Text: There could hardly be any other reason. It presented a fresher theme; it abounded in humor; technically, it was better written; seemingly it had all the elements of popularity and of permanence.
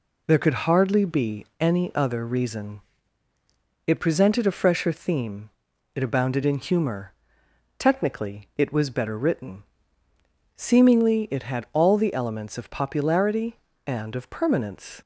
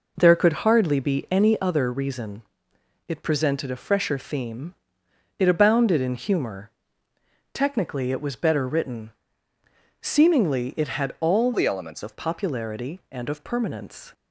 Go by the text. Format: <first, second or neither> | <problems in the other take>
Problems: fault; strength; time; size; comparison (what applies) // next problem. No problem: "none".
first | changes voice from "the" to "elements"; from 11.5 to 12.0 s; 0.5 s long